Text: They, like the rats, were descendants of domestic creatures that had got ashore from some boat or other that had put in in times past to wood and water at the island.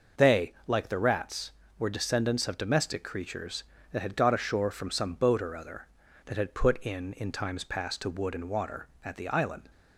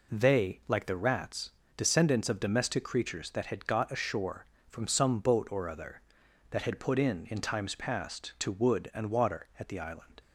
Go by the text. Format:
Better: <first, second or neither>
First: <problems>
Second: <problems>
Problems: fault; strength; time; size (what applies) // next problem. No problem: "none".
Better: first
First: none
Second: skips "were"; at 1.6 s